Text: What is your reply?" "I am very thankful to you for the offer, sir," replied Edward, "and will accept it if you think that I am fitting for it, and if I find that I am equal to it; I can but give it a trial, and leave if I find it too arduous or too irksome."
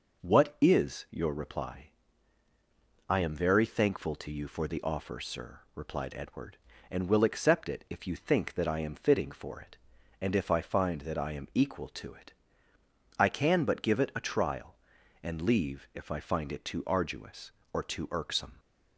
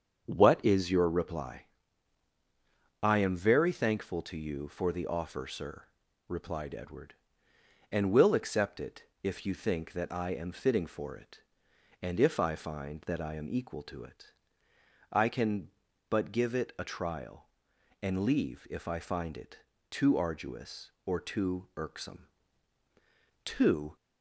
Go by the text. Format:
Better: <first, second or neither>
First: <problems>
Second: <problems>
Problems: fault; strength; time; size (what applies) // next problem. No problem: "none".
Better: first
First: none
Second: starts louder than the rest; strong; until 1.2 s; 7 dB // pauses between "it" and "if"; slight; at 9.0 s; 0.18 s long // pauses between "it" and "too"; slight; at 19.5 s; 0.32 s long // goes on to say "Too"; from 23.4 s on; 0.52 s long